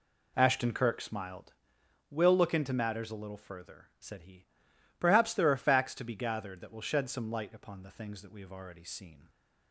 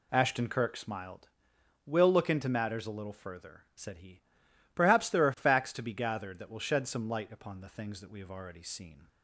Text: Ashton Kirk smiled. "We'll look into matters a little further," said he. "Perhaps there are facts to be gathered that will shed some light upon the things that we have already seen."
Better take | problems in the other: second | starts louder than the rest; slight; until 1.7 s; 2.5 dB

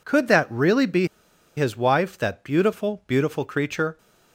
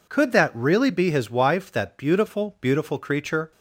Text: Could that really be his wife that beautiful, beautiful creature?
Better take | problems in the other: second | pauses between "be" and "his"; noticeable; at 1.0 s; 0.50 s long

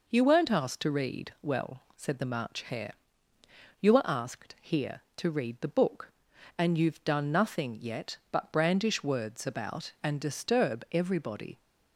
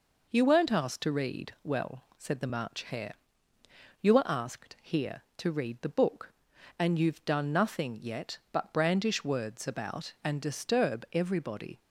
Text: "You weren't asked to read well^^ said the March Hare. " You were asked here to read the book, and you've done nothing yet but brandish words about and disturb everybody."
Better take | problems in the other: neither | none

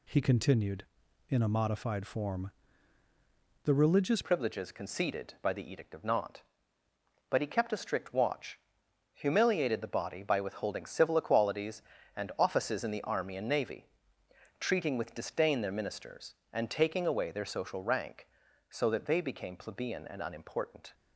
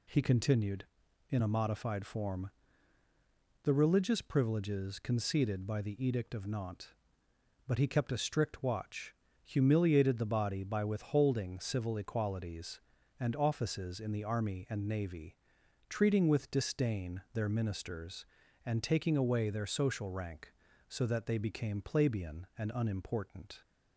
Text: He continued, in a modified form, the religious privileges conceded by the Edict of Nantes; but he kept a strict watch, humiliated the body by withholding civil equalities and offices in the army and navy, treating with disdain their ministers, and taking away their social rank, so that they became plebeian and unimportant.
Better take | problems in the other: second | changes voice at "privileges"; from 4.2 s on; 16.7 s long

